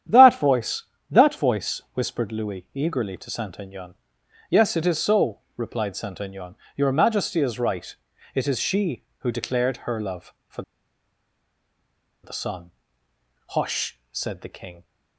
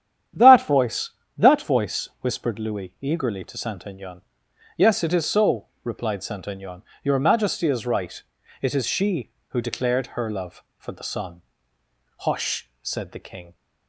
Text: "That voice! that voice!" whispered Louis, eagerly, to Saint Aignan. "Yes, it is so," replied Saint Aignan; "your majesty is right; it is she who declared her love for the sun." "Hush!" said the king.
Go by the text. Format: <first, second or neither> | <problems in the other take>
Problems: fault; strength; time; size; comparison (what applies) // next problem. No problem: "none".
second | starts louder than the rest; strong; until 1.3 s; 9.5 dB; strong in the second // pauses between "for" and "the"; strong; at 10.6 s; 1.6 s long